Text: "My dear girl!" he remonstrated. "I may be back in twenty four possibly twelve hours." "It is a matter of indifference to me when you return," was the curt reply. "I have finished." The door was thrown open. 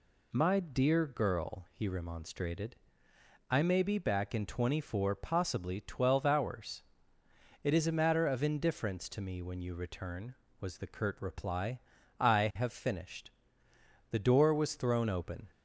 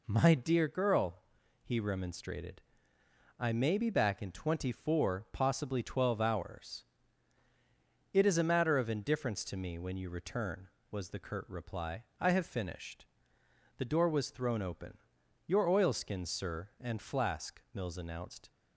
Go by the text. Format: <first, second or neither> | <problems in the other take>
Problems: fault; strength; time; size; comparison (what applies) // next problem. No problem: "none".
first | goes on to say "Your oilskins sir and flask Mills announced"; strong; from 15.4 s on; 3.0 s long